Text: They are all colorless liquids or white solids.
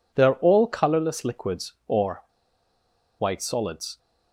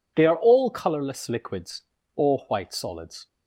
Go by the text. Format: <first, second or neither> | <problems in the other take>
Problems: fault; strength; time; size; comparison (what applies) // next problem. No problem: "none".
second | pauses between "or" and "white"; noticeable; at 2.2 s; 0.96 s long